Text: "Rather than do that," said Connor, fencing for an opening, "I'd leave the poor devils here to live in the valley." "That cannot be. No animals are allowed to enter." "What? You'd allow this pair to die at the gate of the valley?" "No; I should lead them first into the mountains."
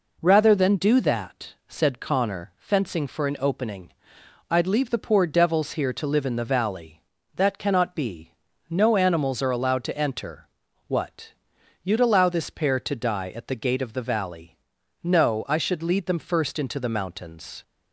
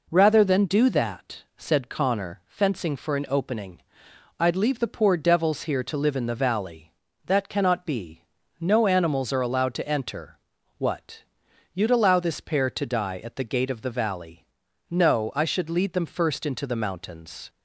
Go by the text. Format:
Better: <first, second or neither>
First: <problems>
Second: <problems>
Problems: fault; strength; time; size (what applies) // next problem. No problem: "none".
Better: neither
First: none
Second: none